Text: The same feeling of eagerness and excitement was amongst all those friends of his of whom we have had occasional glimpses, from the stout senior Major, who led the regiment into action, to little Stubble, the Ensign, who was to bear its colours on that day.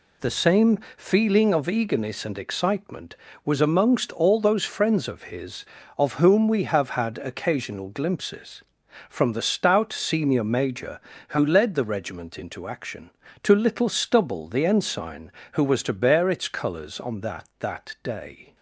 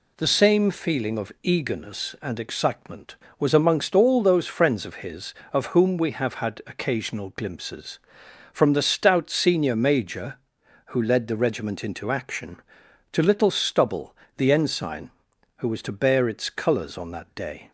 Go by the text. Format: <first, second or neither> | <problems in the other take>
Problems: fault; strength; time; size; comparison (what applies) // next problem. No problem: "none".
second | pauses between "same" and "feeling"; slight; at 0.7 s; 0.18 s long // says "that" twice; at 17.5 s